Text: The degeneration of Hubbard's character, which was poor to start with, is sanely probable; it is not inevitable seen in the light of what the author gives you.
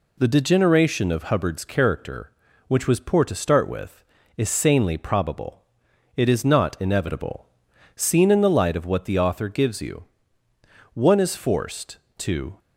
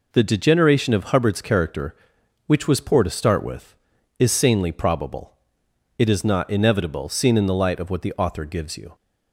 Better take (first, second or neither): second